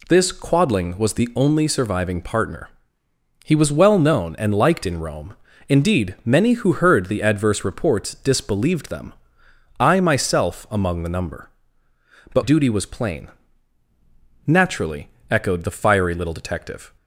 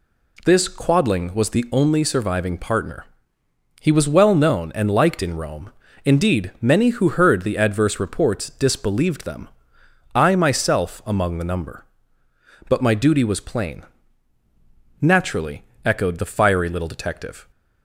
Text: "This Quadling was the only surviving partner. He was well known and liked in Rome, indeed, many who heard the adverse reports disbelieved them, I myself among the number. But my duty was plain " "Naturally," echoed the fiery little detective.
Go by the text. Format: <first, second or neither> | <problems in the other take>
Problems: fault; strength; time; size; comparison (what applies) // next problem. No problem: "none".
second | skips "my"; at 12.4 s